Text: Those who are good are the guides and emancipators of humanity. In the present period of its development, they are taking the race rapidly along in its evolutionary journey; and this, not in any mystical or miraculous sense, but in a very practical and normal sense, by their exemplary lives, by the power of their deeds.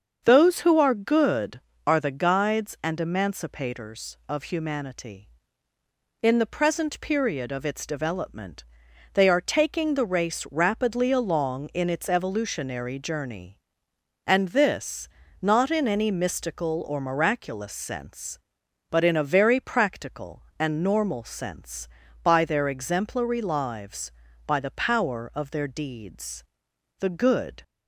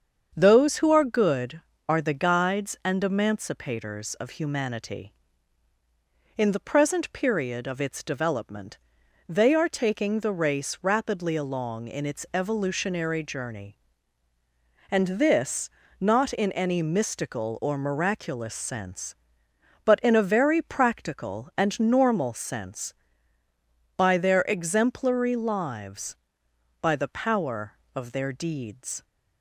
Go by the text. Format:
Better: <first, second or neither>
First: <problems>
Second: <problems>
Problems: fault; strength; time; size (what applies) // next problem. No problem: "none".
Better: second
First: starts louder than the rest; until 1.2 s; 7 dB // goes on to say "The good"; noticeable; from 26.9 s on; 0.64 s long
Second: starts louder than the rest; strong; until 1.3 s; 7.5 dB